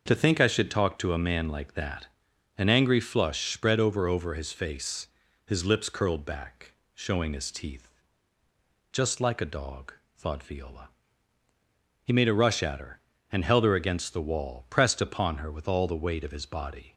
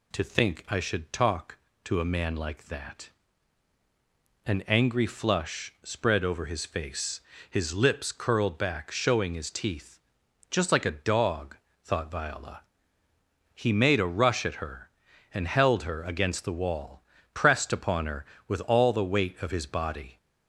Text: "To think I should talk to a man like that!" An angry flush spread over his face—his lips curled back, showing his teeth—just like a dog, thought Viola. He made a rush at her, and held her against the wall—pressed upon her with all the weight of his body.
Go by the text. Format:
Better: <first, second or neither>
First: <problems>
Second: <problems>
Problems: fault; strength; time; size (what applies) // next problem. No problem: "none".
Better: second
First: starts louder than the rest; until 1.0 s; 6 dB // says "over" twice; at 4.0 s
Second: none